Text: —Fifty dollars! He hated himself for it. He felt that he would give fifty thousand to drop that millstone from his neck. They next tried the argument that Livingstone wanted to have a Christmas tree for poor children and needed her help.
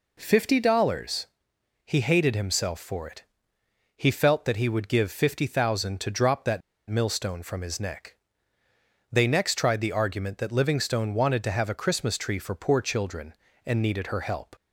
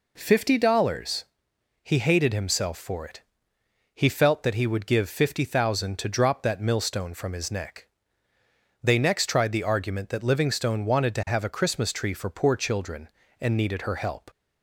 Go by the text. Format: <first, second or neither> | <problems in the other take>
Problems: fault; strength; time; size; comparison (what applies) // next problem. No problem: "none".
second | pauses between "that" and "millstone"; slight; at 6.6 s; 0.28 s long